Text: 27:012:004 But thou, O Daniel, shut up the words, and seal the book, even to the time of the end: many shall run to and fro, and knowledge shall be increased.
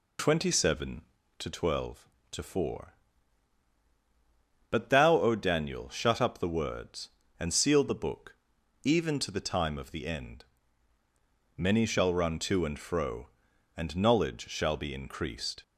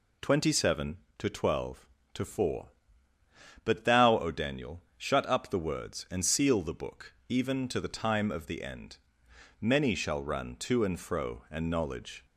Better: first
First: none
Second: stops before "shall be increased"; at 12.2 s

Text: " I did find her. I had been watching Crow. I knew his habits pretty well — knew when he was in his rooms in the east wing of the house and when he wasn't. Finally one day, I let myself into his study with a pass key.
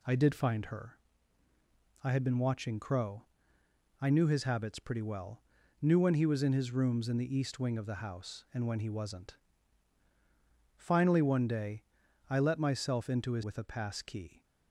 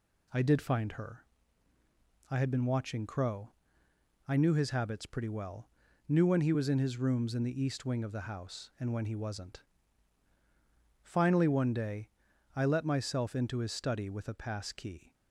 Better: second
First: skips "study"; at 13.4 s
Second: none

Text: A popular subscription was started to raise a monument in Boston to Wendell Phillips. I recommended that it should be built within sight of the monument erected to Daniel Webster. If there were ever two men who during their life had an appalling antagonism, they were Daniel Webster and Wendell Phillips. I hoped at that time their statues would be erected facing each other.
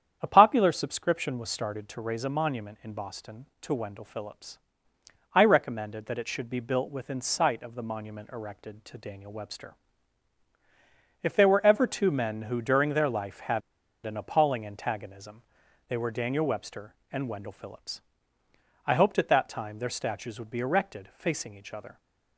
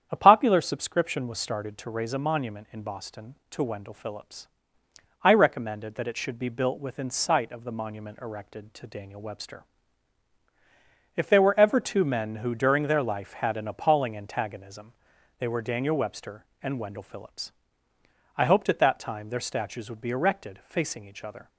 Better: second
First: starts louder than the rest; strong; until 1.2 s; 9 dB // pauses between "had" and "an"; at 13.6 s; 0.43 s long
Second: starts louder than the rest; strong; until 1.1 s; 9 dB

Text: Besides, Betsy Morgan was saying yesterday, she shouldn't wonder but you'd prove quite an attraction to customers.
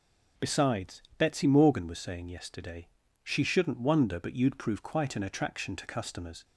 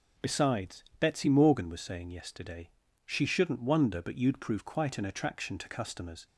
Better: neither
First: none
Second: none

